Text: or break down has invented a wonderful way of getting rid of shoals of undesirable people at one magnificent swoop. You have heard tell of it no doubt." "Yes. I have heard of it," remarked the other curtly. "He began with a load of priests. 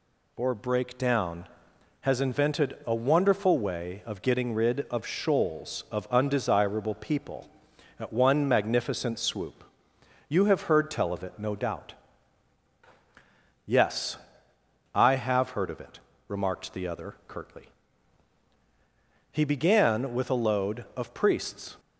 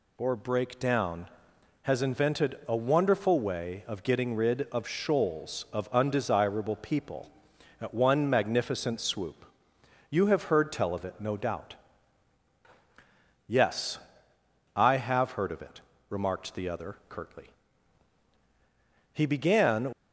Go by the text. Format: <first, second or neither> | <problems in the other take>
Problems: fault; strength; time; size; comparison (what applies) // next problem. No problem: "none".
first | stops before "with a load of priests"; at 19.9 s